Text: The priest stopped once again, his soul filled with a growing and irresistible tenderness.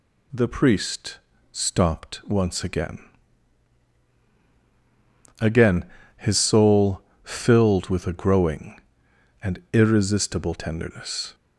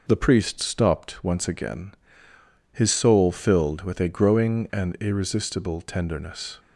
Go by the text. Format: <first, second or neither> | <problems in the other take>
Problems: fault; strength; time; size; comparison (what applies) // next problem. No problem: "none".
second | pauses between "priest" and "stopped"; slight; at 1.1 s; 0.32 s long // says "again" twice; at 5.3 s // pauses between "soul" and "filled"; slight; at 6.9 s; 0.24 s long